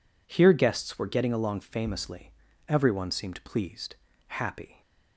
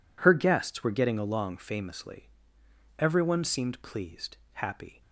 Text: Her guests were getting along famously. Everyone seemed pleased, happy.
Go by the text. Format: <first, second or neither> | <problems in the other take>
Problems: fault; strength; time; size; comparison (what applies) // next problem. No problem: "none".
second | says "Here" for "Her"; at 0.2 s